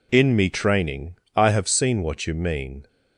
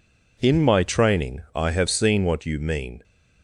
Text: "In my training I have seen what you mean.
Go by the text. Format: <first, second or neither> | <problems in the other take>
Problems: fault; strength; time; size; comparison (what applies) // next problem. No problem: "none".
second | says "me" for "my"; at 0.3 s // pauses between "training" and "I"; slight; at 1.1 s; 0.18 s long